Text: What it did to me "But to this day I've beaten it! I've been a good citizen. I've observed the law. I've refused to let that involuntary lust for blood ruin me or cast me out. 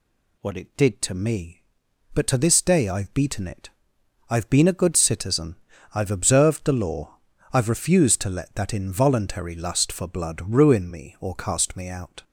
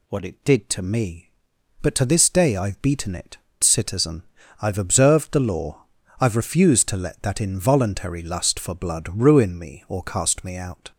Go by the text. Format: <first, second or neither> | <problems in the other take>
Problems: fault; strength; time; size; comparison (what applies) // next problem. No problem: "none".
first | skips "I've been a good"; at 3.5 s